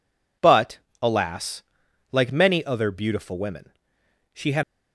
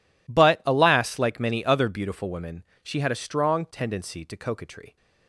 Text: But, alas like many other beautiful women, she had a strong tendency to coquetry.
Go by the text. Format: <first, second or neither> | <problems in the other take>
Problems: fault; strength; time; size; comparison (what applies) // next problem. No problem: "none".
second | pauses between "alas" and "like"; noticeable; at 1.6 s; 0.48 s long // stops before "a strong tendency to coquetry"; at 4.6 s